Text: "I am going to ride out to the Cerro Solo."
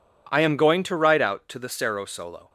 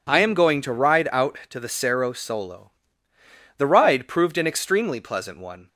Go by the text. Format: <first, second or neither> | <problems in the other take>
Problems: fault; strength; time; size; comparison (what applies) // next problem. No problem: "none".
first | goes on to say "The ride proved an extremely pleasant one"; strong; from 3.5 s on; 2.1 s long